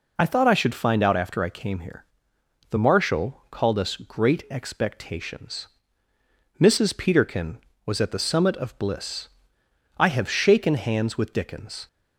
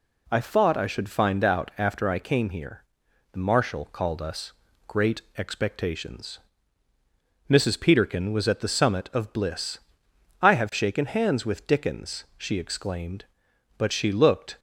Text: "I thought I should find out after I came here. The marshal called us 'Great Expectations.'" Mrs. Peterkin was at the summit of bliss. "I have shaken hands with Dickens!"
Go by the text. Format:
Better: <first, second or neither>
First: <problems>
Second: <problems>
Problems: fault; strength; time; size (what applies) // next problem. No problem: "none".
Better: first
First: none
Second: pauses between "us" and "Great"; at 4.5 s; 0.38 s long // pauses between "Great" and "Expectations"; slight; at 5.2 s; 0.16 s long // goes on to say "she exclaimed But she looked"; strong; from 12.3 s on; 2.2 s long